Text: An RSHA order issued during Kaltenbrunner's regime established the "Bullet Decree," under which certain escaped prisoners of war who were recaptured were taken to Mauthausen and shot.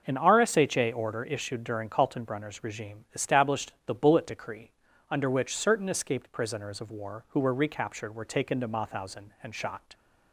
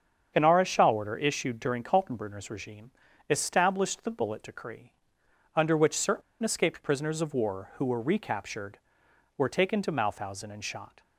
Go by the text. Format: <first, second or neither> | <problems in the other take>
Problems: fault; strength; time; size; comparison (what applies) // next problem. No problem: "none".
first | starts louder than the rest; strong; until 1.3 s; 7.5 dB; noticeable in the first // pauses between "regime" and "established"; at 2.9 s; 0.38 s long // pauses between "certain" and "escaped"; slight; at 6.2 s; 0.21 s long